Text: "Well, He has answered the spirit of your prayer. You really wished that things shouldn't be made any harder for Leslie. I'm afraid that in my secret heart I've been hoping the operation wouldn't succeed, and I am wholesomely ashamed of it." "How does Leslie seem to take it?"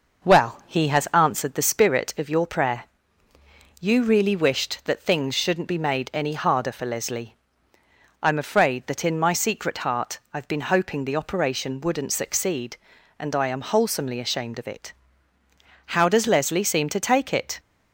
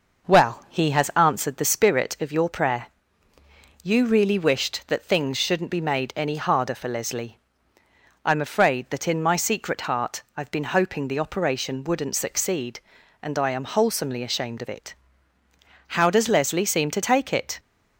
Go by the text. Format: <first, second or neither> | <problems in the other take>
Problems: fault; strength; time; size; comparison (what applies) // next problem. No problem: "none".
neither | none